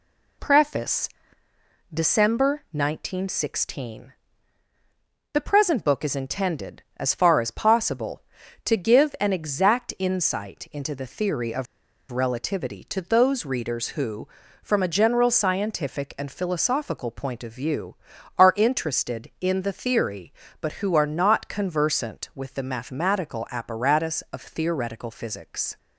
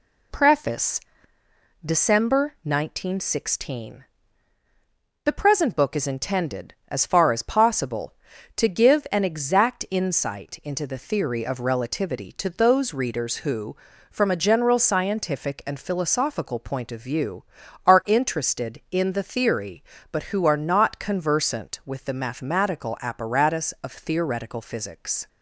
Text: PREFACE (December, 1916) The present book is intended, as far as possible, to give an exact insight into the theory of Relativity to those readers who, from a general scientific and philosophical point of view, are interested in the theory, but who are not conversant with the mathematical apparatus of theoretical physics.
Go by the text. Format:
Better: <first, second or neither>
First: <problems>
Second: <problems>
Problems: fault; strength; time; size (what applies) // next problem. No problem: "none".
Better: second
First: pauses between "of" and "Relativity"; at 11.6 s; 0.45 s long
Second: none